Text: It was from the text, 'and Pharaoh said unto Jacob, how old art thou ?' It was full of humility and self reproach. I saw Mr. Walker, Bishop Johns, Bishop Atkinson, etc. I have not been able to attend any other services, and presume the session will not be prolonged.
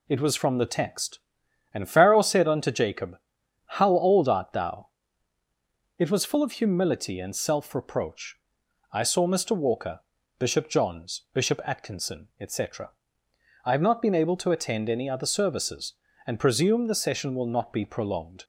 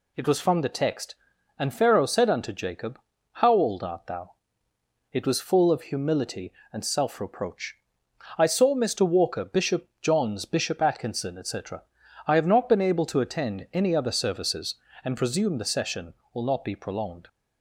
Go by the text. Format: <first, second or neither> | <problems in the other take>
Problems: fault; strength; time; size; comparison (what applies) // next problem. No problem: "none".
neither | none